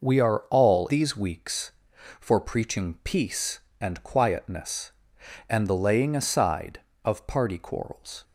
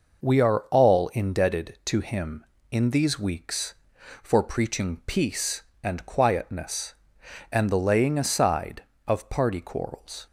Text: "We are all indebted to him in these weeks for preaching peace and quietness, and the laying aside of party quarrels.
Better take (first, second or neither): second